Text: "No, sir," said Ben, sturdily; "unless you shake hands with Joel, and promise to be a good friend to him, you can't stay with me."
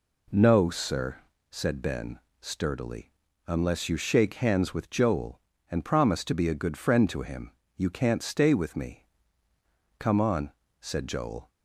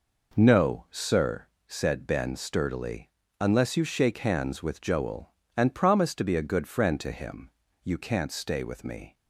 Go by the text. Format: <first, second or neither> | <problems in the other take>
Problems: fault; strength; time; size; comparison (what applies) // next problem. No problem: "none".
second | goes on to say "Come on said Joel"; from 9.9 s on; 1.5 s long